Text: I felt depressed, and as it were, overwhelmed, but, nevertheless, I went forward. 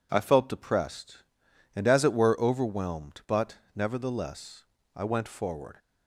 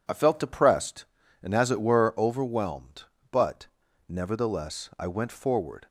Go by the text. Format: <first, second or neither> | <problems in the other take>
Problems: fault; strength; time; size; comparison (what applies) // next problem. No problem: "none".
neither | none